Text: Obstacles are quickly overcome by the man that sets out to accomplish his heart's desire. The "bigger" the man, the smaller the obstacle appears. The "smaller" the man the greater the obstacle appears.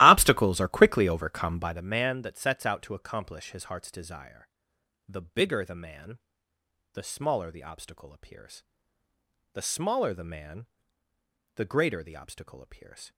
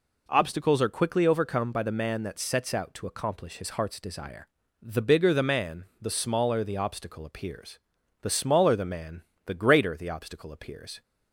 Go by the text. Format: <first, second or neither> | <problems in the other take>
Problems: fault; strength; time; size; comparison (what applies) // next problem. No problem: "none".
second | starts louder than the rest; strong; until 1.9 s; 16 dB // pauses between "man" and "the"; noticeable; at 10.6 s; 0.88 s long; slight in the second